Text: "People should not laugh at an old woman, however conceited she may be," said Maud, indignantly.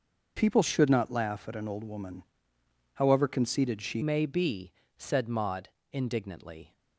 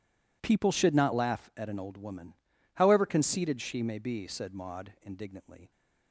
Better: second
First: changes voice at "may"; from 4.0 s on; 2.7 s long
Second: none

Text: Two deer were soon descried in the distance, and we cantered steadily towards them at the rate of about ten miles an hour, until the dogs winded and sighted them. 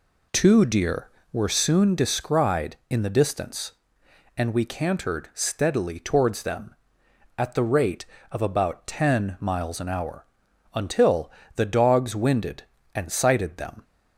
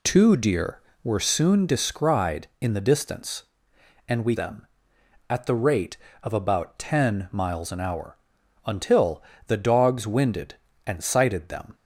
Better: first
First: pauses between "until" and "the"; slight; at 11.3 s; 0.24 s long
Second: skips "cantered steadily towards"; at 4.3 s // pauses between "until" and "the"; slight; at 9.2 s; 0.24 s long

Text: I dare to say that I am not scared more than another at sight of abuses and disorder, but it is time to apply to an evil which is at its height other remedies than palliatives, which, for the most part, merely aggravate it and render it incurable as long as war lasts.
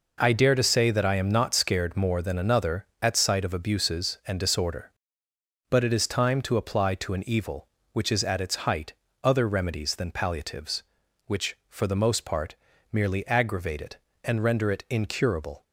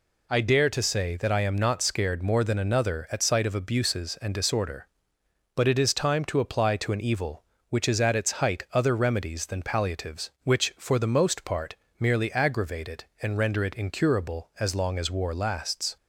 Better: second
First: pauses between "height" and "other"; slight; at 8.9 s; 0.30 s long // stops before "as long as war lasts"; at 15.6 s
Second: none

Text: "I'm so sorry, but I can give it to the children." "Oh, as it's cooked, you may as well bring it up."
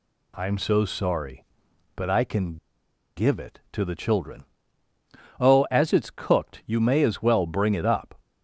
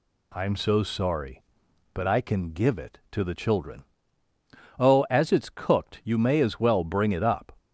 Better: second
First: pauses between "can" and "give"; noticeable; at 2.5 s; 0.60 s long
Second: none

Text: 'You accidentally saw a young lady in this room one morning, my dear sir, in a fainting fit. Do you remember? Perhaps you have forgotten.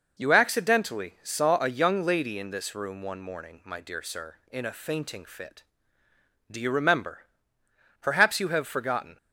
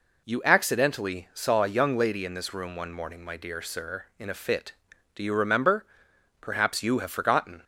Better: first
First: none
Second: skips "fainting"; at 4.3 s

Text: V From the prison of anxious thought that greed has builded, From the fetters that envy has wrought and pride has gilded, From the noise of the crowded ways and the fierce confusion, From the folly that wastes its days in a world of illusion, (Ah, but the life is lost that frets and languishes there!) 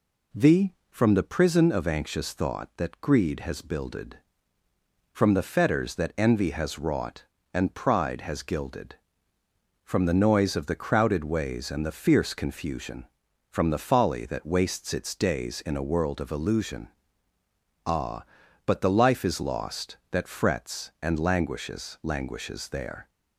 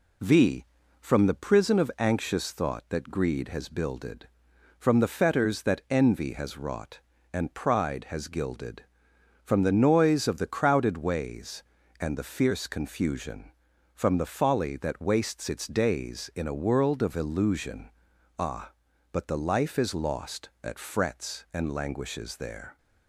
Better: second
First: says "languishes" twice; at 22.0 s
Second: none

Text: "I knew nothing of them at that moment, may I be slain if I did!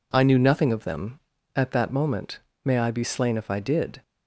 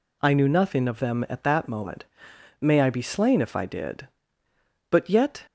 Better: first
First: none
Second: goes on to say "but yet"; from 4.9 s on; 0.54 s long

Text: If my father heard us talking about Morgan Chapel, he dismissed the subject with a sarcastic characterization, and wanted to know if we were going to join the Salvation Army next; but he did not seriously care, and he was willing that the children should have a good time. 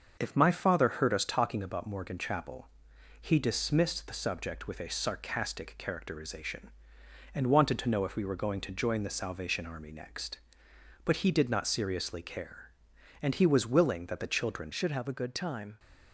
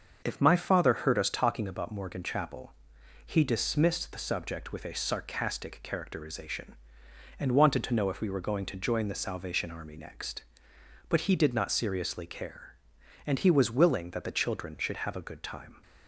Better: second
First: starts louder than the rest; until 1.2 s; 6.5 dB // changes voice at "should"; from 14.7 s on; 1.0 s long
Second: starts louder than the rest; until 1.2 s; 6.5 dB

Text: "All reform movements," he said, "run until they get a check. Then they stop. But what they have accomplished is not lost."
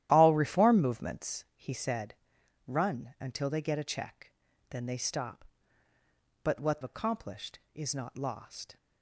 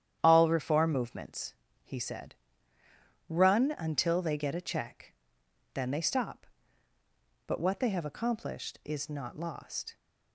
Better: second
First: starts louder than the rest; strong; until 1.1 s; 12.5 dB // skips "they have"; at 6.8 s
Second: starts louder than the rest; strong; until 1.2 s; 10 dB

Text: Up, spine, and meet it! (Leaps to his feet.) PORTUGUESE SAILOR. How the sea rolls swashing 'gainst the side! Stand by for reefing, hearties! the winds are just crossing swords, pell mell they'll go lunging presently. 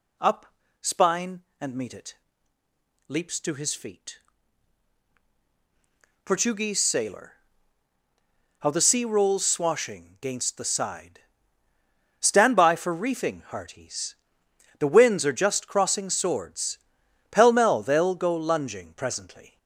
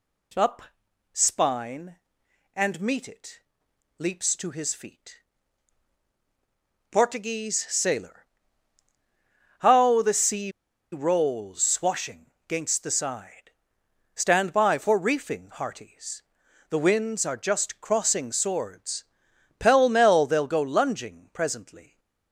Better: first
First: none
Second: pauses between "sea" and "rolls"; at 10.5 s; 0.41 s long // pauses between "swashing" and "gainst"; slight; at 12.3 s; 0.16 s long

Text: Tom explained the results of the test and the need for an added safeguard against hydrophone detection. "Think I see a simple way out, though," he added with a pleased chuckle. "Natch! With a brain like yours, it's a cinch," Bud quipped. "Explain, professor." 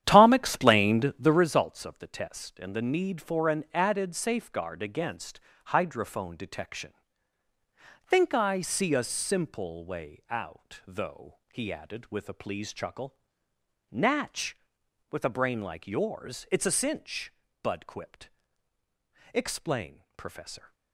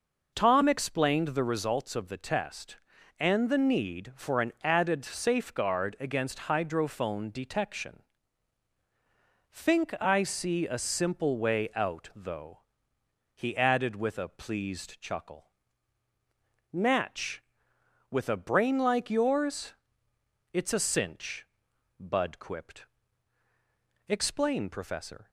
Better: second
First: starts louder than the rest; strong; until 1.5 s; 10.5 dB // pauses between "against" and "hydrophone"; slight; at 5.3 s; 0.26 s long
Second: none

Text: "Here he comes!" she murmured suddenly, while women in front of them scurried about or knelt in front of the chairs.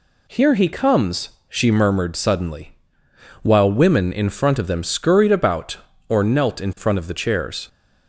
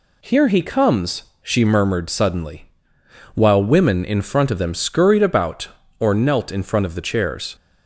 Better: neither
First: none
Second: none

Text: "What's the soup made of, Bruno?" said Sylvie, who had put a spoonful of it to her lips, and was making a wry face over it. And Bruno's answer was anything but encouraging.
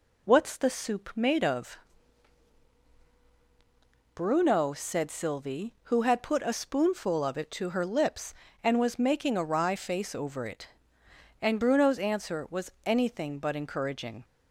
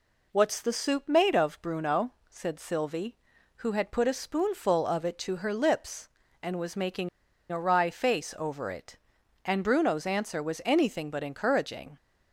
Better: first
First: none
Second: pauses between "making" and "a"; at 7.0 s; 0.41 s long

